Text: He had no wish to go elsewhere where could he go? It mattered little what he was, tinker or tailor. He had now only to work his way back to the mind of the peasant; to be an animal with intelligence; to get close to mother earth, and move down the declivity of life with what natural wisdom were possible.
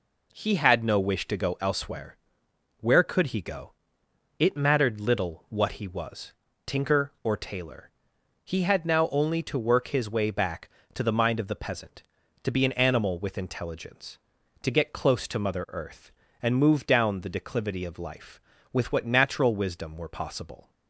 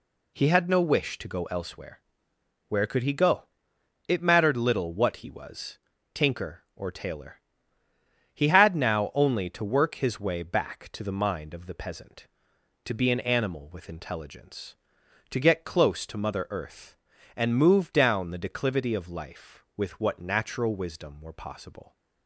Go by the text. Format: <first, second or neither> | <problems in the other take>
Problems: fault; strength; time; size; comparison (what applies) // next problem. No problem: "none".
neither | pauses between "elsewhere" and "where"; noticeable; the same in both